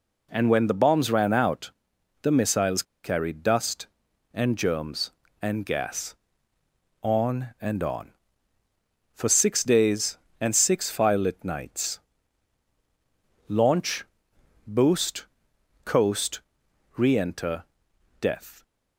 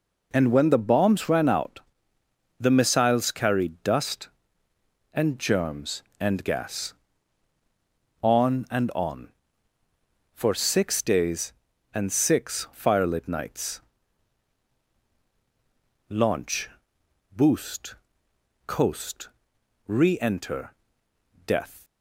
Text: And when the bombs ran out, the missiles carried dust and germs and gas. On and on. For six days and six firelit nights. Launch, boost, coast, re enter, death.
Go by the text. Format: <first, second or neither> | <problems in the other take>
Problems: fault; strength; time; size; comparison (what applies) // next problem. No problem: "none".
second | pauses between "missiles" and "carried"; slight; at 2.8 s; 0.20 s long